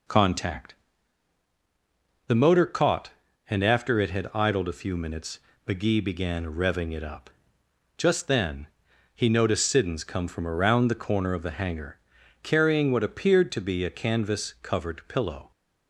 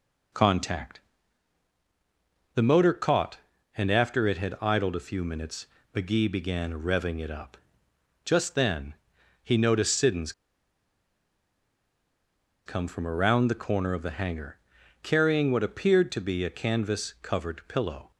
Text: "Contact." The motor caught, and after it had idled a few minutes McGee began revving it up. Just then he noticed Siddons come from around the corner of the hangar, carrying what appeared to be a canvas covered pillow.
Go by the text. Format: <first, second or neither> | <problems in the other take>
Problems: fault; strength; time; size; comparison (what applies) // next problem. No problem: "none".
first | pauses between "minutes" and "McGee"; slight; at 5.6 s; 0.26 s long; slight in the first // pauses between "then" and "he"; noticeable; at 8.9 s; 0.48 s long; noticeable in the first // pauses between "Siddons" and "come"; strong; at 10.3 s; 2.3 s long